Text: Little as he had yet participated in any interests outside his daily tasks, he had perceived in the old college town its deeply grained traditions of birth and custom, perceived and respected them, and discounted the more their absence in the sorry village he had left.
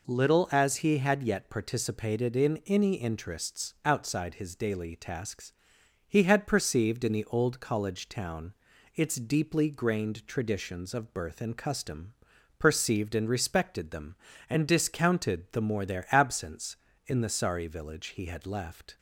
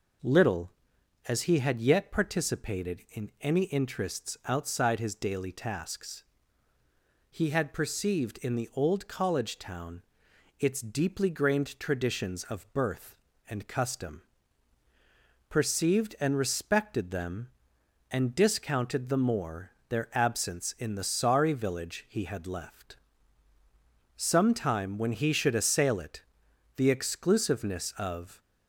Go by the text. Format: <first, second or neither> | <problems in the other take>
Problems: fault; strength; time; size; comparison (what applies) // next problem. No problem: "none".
first | pauses between "town" and "its"; noticeable; at 10.0 s; 0.56 s long; also in the first // pauses between "more" and "their"; slight; at 19.6 s; 0.18 s long // goes on to say "Sometime when he should assail it the exclusiveness of"; strong; from 24.1 s on; 4.2 s long